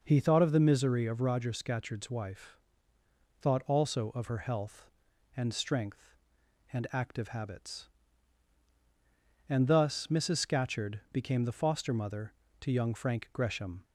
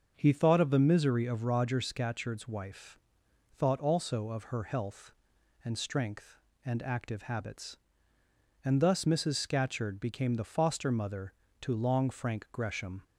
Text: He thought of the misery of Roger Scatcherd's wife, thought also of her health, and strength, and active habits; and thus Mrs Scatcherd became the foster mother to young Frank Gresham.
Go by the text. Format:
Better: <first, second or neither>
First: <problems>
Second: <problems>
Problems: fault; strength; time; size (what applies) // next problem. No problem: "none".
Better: first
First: none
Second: starts louder than the rest; until 1.1 s; 6.5 dB // says "long" for "young"; at 11.7 s